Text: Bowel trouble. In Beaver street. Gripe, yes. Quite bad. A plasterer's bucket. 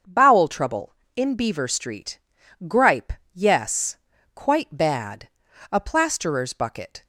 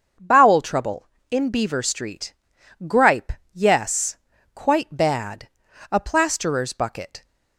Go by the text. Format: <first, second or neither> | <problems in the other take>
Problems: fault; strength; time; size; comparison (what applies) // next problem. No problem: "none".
neither | starts louder than the rest; the same in both